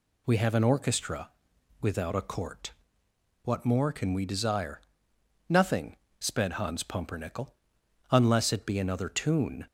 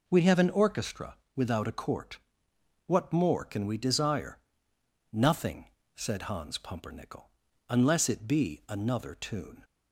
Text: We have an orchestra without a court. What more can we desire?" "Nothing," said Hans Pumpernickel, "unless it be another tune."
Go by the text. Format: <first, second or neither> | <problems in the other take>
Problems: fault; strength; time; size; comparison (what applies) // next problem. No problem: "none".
second | pauses between "orchestra" and "without"; noticeable; at 1.3 s; 0.50 s long; slight in the second // says "sped" for "said"; at 6.1 s